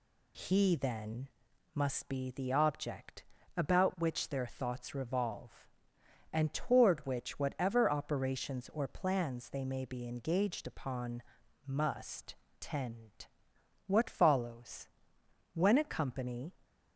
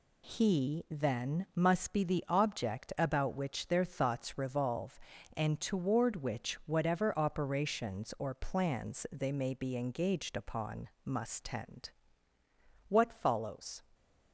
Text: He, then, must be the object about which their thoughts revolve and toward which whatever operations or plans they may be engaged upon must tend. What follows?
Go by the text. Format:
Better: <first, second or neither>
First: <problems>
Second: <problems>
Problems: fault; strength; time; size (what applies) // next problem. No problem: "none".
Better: second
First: pauses between "object" and "about"; slight; at 3.2 s; 0.32 s long // pauses between "upon" and "must"; at 11.2 s; 0.42 s long // pauses between "must" and "tend"; slight; at 12.3 s; 0.24 s long // goes on to say "When a company"; noticeable; from 15.5 s on; 1.0 s long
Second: pauses between "upon" and "must"; slight; at 10.8 s; 0.16 s long